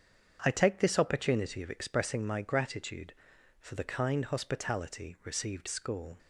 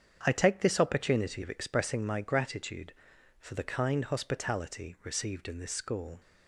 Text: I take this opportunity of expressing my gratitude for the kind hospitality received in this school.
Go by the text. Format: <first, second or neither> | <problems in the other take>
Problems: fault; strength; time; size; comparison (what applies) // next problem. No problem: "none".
second | starts louder than the rest; strong; until 1.4 s; 7.5 dB; strong in the second // skips "in this"; at 5.6 s